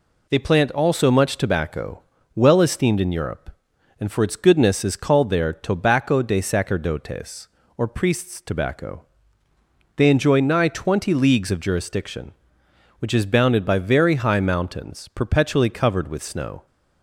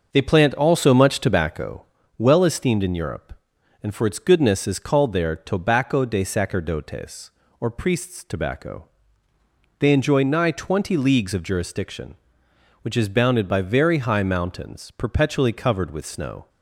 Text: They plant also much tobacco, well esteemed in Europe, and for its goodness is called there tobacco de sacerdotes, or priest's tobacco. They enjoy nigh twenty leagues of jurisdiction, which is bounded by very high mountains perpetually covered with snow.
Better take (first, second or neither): first